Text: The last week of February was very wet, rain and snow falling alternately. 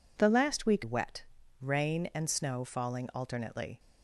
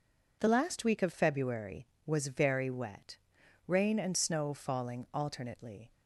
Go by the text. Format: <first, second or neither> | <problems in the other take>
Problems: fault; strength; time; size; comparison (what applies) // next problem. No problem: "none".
second | skips "of February was very"; at 0.8 s